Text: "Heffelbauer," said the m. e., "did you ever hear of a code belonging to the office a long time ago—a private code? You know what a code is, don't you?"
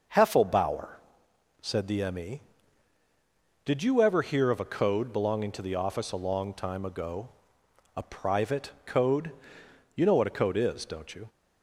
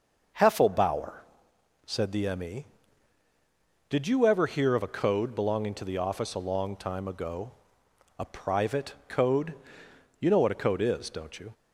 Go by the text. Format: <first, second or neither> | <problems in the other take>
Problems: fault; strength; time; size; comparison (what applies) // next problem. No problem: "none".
neither | starts louder than the rest; the same in both // pauses between "private" and "code"; slight; the same in both